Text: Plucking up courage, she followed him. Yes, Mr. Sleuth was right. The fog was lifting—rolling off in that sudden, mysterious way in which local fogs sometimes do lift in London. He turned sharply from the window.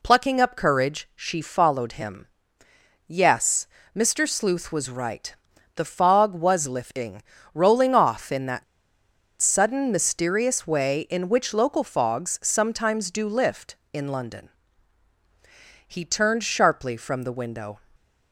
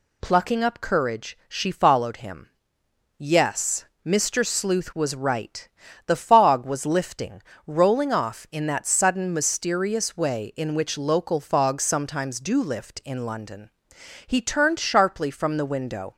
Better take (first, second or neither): second